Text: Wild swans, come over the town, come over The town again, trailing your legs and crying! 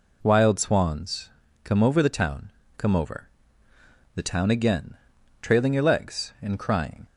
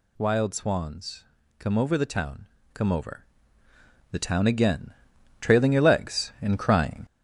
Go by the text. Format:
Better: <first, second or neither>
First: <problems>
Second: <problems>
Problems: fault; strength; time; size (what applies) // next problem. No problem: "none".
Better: first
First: pauses between "over" and "The"; noticeable; at 3.2 s; 0.86 s long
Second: gets louder; noticeable; throughout; 4.5 dB // pauses between "over" and "The"; noticeable; at 3.2 s; 0.86 s long